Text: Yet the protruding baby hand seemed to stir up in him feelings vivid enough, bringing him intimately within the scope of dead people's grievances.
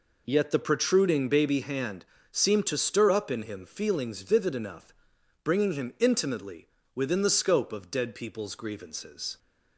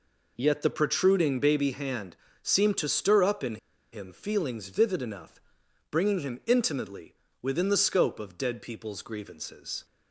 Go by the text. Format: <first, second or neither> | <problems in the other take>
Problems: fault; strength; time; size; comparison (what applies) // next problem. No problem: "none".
first | pauses between "hand" and "seemed"; slight; at 2.1 s; 0.28 s long; slight in the first // pauses between "in" and "him"; slight; at 3.5 s; 0.36 s long // pauses between "intimately" and "within"; slight; at 7.1 s; 0.26 s long; slight in the first